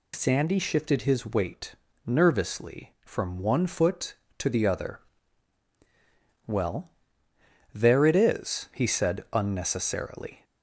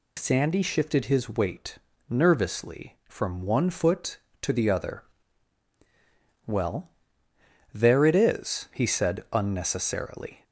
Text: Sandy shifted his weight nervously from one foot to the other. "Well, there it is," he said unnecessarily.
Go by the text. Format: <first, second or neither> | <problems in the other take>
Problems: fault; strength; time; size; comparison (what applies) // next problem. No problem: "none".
neither | pauses between "weight" and "nervously"; slight; the same in both